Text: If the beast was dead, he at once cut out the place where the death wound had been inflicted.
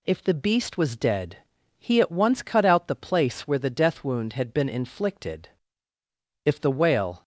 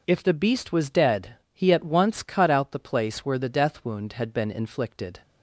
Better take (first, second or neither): second